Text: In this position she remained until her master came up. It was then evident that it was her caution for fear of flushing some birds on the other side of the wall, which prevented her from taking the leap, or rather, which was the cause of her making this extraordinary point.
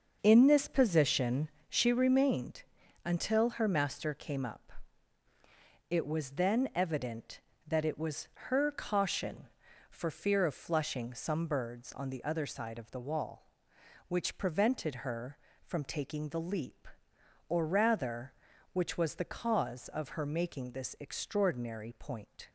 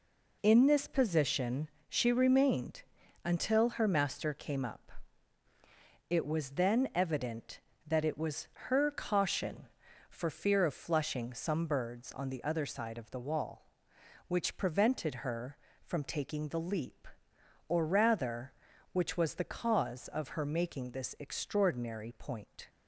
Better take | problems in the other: second | starts louder than the rest; until 2.0 s; 6.5 dB // pauses between "position" and "she"; slight; at 1.4 s; 0.20 s long; slight in the second // pauses between "remained" and "until"; at 2.6 s; 0.42 s long; also in the second // pauses between "was" and "her"; slight; at 8.2 s; 0.22 s long; slight in the second

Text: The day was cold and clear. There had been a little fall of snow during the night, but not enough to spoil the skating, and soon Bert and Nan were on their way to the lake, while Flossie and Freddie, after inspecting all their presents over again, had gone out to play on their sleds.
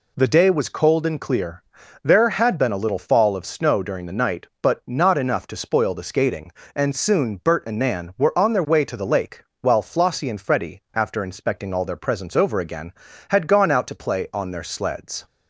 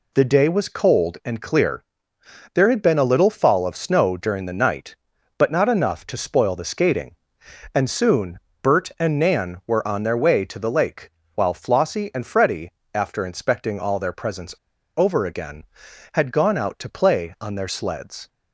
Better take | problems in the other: first | pauses between "soon" and "Bert"; slight; at 8.3 s; 0.22 s long // pauses between "presents" and "over"; at 14.5 s; 0.41 s long

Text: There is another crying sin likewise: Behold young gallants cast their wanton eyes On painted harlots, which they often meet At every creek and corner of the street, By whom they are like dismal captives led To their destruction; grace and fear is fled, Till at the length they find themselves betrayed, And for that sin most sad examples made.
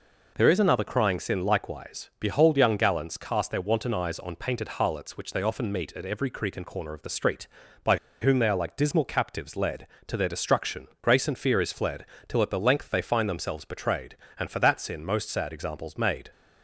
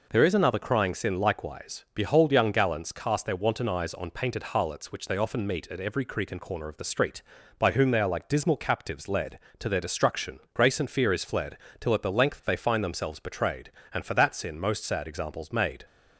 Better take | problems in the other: second | pauses between "By" and "whom"; slight; at 7.9 s; 0.23 s long

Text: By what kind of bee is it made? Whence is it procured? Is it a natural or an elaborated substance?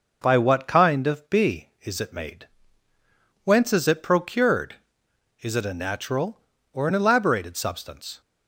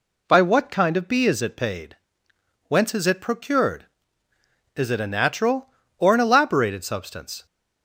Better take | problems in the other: first | says "paid" for "made"; at 1.5 s

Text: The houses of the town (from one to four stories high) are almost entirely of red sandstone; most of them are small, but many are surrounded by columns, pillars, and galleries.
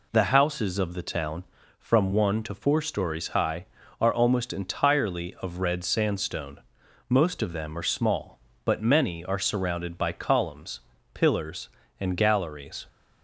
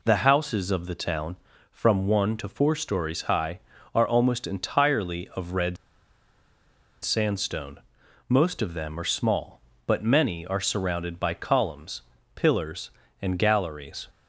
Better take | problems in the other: first | pauses between "red" and "sandstone"; strong; at 5.7 s; 1.2 s long

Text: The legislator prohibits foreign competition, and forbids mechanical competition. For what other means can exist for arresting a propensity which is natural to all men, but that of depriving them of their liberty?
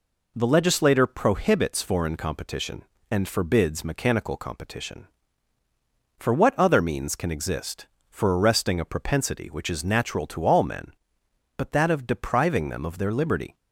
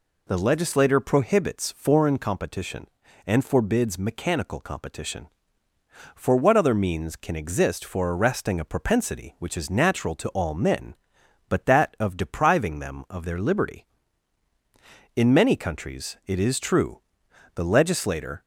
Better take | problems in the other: first | goes on to say "In many countries it is true the legislator"; strong; from 15.1 s on; 3.2 s long

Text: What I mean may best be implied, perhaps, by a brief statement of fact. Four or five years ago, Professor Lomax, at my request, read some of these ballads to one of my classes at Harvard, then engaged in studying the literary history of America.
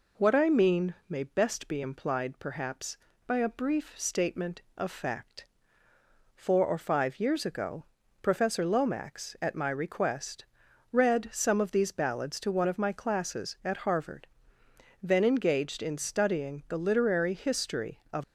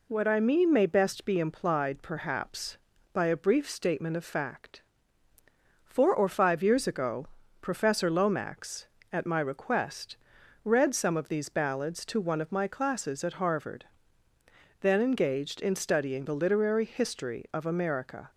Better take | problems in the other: second | pauses between "mean" and "may"; slight; at 0.9 s; 0.16 s long // stops before "America"; at 18.2 s

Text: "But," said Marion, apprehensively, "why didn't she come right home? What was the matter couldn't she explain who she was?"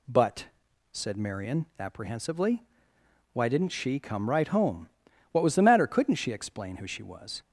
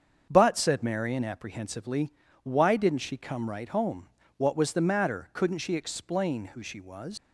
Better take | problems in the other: first | starts louder than the rest; strong; until 1.3 s; 7 dB // leaves "was" unfinished; at 7.1 s; 125 ms

